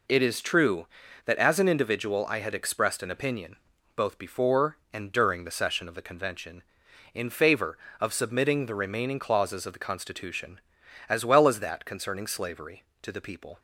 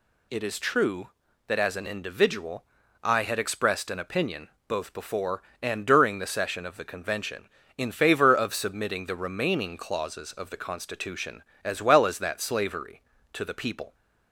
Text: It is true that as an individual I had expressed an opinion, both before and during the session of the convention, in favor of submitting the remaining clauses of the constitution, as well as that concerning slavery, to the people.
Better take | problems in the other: first | pauses between "individual" and "I"; at 2.6 s; 0.38 s long // skips "concerning"; at 12.3 s

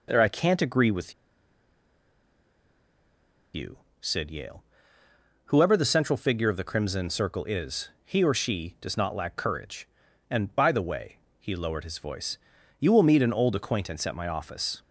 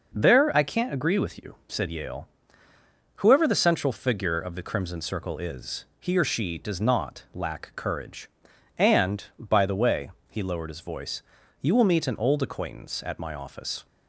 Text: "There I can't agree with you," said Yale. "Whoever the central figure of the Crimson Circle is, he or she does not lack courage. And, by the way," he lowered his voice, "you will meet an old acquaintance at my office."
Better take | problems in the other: second | pauses between "with" and "you"; strong; at 1.1 s; 2.4 s long

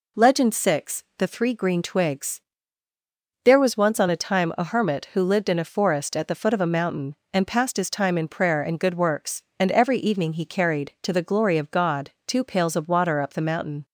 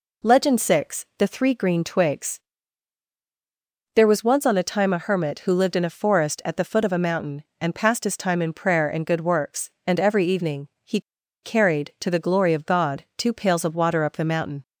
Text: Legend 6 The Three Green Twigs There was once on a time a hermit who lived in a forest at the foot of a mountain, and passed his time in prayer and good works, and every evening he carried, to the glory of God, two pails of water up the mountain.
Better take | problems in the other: first | pauses between "Twigs" and "There"; strong; at 2.3 s; 1.5 s long; also in the first // pauses between "evening" and "he"; slight; at 10.6 s; 0.16 s long // pauses between "he" and "carried"; at 10.9 s; 0.43 s long

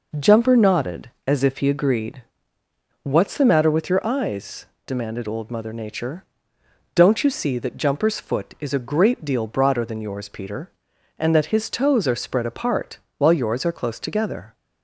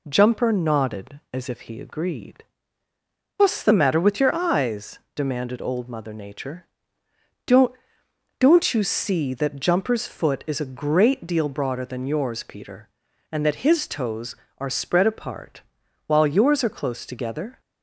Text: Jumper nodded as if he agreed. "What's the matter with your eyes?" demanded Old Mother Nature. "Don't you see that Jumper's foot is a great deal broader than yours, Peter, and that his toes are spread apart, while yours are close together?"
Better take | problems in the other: first | says "Don't" twice; at 8.3 s

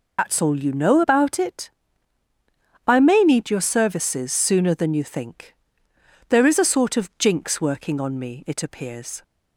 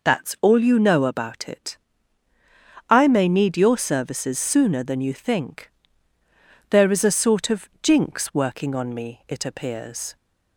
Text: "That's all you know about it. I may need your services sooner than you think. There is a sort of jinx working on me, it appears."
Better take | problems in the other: second | loses the start of "That's"; at 0.1 s; 70 ms

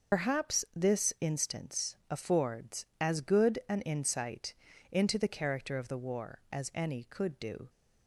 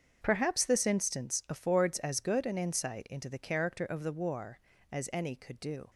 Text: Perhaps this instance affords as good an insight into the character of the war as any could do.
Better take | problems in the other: second | loses the start of "Perhaps"; at 0.1 s; 85 ms // starts louder than the rest; until 1.3 s; 6 dB; strong in the second // pauses between "insight" and "into"; at 4.5 s; 0.38 s long

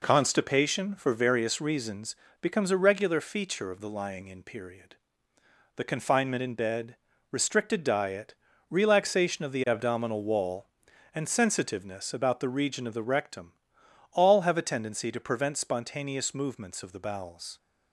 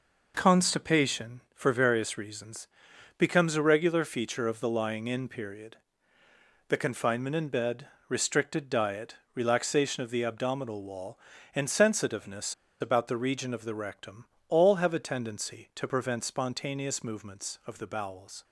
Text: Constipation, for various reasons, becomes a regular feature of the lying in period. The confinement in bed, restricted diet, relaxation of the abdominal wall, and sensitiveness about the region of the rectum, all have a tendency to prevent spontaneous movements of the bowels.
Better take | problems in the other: first | pauses between "sensitiveness" and "about"; slight; at 12.5 s; 0.26 s long

